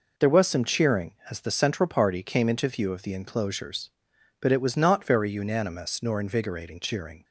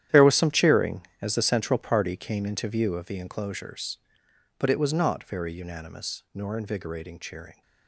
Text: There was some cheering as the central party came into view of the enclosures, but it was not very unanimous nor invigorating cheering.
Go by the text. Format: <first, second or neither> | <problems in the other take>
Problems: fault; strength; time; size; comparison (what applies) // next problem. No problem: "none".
first | gets quieter; strong; throughout; 14 dB